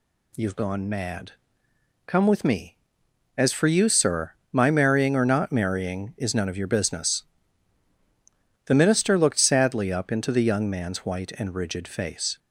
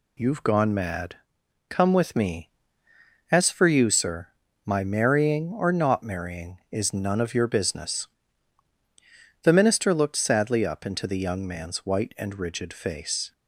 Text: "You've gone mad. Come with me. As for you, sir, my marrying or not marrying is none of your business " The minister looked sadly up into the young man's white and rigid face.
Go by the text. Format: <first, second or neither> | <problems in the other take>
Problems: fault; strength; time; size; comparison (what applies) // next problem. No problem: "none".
neither | none